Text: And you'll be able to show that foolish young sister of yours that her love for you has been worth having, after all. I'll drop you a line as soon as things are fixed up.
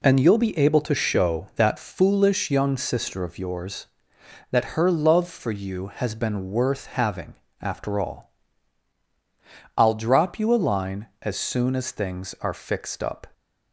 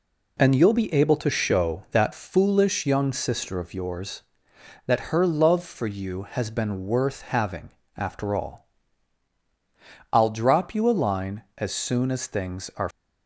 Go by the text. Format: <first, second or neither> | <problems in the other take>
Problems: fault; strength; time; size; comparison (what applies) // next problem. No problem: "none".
first | stops before "fixed up"; at 12.9 s